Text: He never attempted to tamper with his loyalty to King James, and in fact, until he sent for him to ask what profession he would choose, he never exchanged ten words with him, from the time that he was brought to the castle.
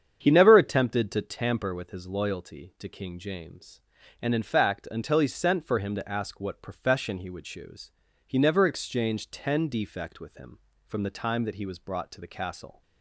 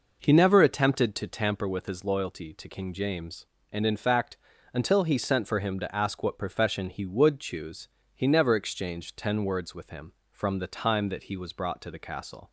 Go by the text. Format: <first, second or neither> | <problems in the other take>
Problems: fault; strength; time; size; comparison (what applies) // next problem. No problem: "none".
second | starts louder than the rest; strong; until 1.2 s; 8 dB // says "defect" for "words"; at 9.6 s